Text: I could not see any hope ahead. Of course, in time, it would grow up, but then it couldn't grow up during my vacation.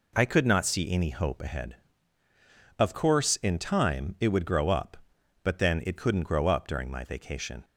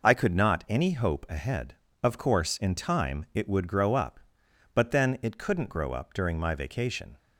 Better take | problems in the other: first | skips "see"; at 0.6 s

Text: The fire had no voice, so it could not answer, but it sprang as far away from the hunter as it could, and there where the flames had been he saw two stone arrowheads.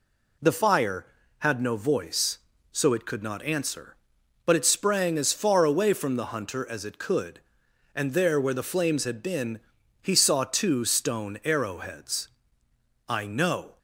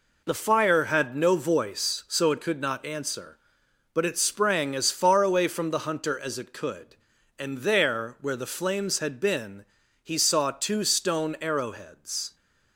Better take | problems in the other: second | pauses between "been" and "he"; at 9.5 s; 0.42 s long; slight in the second // goes on to say "I know"; noticeable; from 13.0 s on; 0.70 s long

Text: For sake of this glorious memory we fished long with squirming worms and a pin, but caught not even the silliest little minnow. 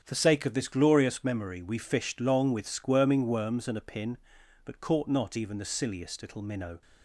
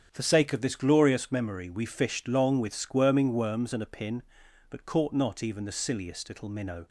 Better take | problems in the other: neither | starts louder than the rest; strong; the same in both

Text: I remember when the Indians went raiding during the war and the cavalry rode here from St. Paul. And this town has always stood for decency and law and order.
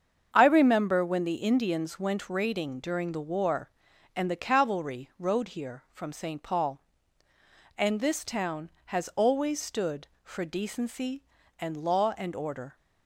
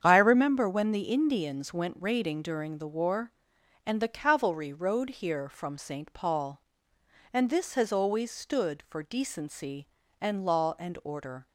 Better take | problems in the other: first | starts louder than the rest; strong; until 1.0 s; 8 dB; strong in the first // skips "town"; at 7.7 s

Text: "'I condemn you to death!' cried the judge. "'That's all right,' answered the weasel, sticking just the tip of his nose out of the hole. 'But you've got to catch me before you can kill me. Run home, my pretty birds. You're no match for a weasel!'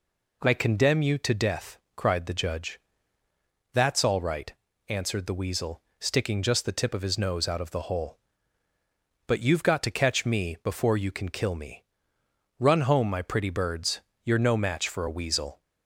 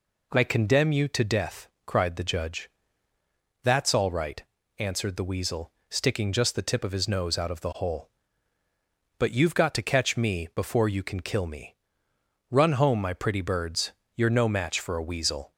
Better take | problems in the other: neither | none

